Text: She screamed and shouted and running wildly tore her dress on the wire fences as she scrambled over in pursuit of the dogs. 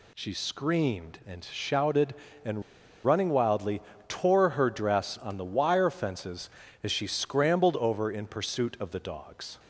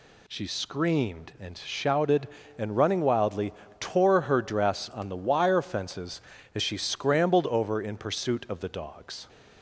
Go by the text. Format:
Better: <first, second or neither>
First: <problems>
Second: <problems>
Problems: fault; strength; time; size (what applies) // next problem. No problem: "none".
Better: second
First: pauses between "and" and "running"; at 2.6 s; 0.42 s long // pauses between "wildly" and "tore"; slight; at 3.8 s; 0.26 s long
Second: pauses between "wildly" and "tore"; slight; at 3.5 s; 0.26 s long